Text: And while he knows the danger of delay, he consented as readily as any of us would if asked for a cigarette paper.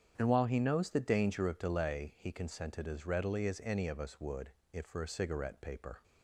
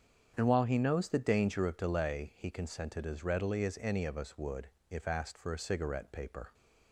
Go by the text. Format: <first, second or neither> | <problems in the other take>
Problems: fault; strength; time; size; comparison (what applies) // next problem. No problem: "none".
second | starts louder than the rest; strong; until 1.1 s; 8 dB; strong in the second // pauses between "would" and "if"; slight; at 4.5 s; 0.22 s long; slight in the second // skips "asked"; at 4.8 s